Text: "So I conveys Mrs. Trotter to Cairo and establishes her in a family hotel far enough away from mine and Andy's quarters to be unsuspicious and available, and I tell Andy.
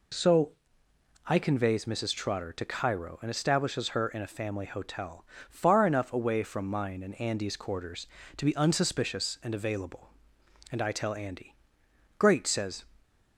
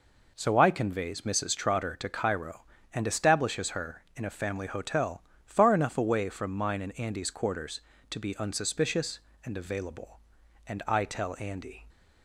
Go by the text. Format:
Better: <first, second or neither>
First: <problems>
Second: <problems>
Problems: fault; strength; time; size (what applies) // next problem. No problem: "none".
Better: second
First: pauses between "So" and "I"; noticeable; at 0.5 s; 0.72 s long // pauses between "hotel" and "far"; slight; at 5.2 s; 0.24 s long // goes on to say "Great says"; noticeable; from 12.1 s on; 0.66 s long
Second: pauses between "hotel" and "far"; slight; at 5.2 s; 0.24 s long